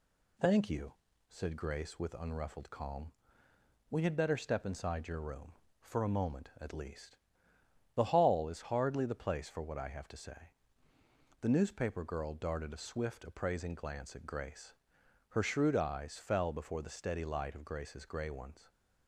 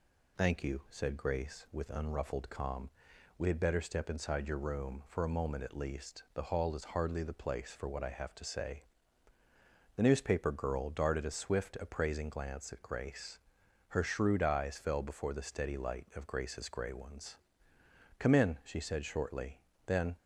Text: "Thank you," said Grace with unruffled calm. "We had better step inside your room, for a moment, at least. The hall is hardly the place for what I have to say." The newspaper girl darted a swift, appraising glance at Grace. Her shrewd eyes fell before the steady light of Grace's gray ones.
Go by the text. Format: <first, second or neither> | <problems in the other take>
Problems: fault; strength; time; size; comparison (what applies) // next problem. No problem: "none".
first | goes on to say "Come in she said shortly then"; strong; from 18.1 s on; 1.9 s long